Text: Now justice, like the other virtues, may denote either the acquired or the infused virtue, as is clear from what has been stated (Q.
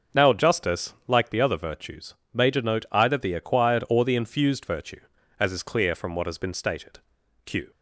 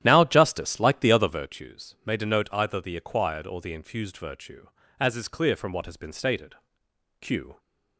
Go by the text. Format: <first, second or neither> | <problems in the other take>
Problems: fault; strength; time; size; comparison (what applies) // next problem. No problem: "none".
first | starts louder than the rest; strong; until 1.6 s; 11.5 dB